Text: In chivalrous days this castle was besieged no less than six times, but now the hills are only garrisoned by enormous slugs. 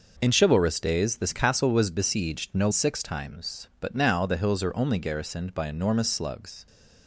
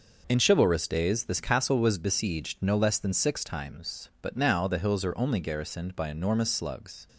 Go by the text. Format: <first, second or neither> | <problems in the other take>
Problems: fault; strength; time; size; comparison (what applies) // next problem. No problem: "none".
second | skips "less than"; at 2.6 s